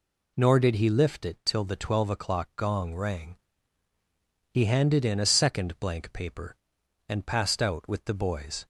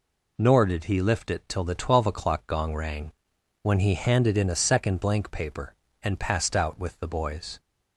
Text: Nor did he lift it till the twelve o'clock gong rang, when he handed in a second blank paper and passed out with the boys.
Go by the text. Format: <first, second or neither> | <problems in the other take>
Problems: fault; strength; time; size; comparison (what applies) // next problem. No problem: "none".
second | skips "when"; at 3.9 s